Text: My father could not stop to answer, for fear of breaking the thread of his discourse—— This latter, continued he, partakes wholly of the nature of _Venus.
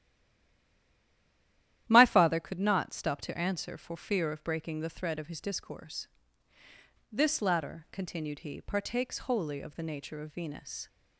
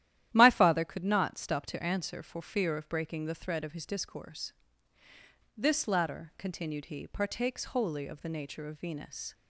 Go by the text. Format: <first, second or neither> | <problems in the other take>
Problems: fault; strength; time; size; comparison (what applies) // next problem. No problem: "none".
second | stays silent before the first word; noticeable; until 1.8 s; 1.8 s long // starts louder than the rest; strong; until 2.8 s; 12.5 dB; strong in the second